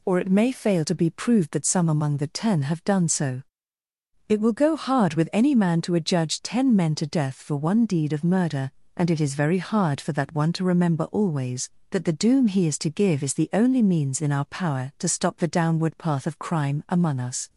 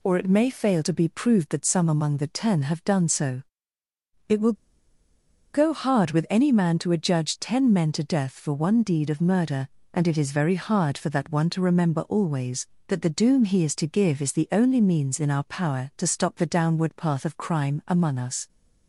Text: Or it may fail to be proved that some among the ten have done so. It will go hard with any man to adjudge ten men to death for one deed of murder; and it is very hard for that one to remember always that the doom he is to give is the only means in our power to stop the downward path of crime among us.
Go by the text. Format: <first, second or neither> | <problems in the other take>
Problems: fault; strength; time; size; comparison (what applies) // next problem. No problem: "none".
first | pauses between "will" and "go"; at 4.5 s; 1.0 s long